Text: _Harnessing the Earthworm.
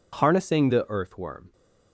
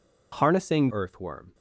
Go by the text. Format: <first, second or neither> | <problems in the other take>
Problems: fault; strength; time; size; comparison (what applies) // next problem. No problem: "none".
first | skips "the"; at 0.9 s